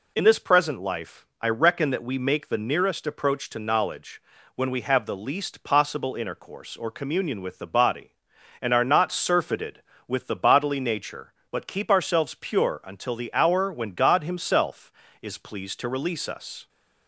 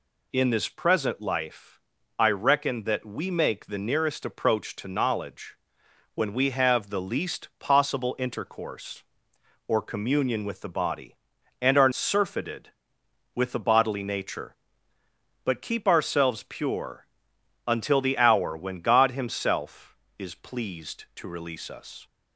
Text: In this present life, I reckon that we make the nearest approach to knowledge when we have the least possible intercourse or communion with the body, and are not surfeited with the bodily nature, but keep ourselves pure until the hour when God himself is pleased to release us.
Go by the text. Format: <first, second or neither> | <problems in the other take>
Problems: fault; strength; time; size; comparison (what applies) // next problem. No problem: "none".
first | pauses between "knowledge" and "when"; noticeable; at 5.5 s; 0.60 s long; slight in the first // skips "not"; at 11.9 s // pauses between "pure" and "until"; noticeable; at 17.0 s; 0.60 s long